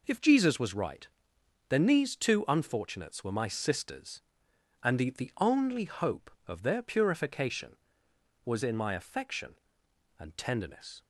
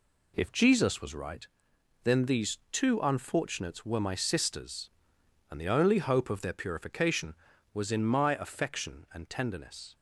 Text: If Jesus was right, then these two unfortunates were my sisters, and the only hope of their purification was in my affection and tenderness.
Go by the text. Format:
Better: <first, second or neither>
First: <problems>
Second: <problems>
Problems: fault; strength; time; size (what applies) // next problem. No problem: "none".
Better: second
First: says "the" twice; at 5.1 s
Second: none